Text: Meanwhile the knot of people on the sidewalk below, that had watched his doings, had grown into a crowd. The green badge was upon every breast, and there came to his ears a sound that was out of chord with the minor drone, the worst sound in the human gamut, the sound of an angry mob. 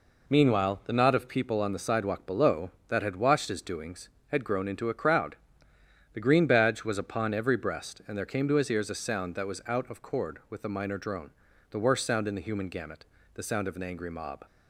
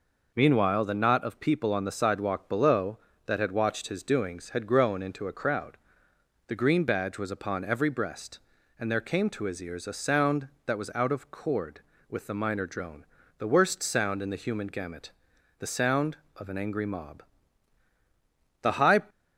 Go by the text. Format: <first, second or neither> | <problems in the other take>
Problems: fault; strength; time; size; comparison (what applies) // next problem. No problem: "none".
first | goes on to say "The high"; slight; from 18.6 s on; 0.40 s long